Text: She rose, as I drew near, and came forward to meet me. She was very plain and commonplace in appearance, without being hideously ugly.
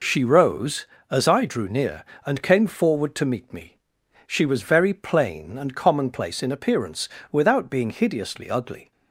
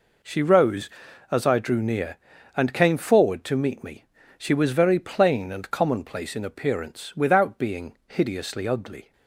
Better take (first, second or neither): neither